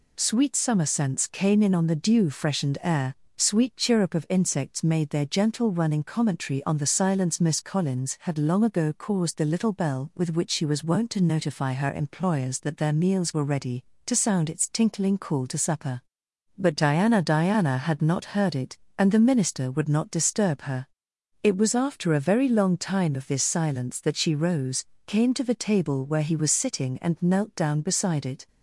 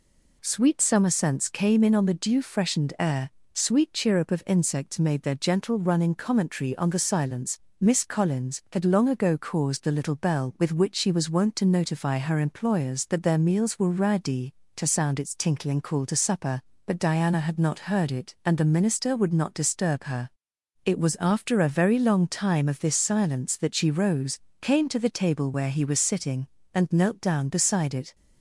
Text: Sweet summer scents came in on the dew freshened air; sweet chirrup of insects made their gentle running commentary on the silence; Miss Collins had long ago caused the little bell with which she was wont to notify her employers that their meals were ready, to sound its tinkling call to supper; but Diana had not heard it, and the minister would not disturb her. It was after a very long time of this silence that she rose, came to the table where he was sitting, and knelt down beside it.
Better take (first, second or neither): second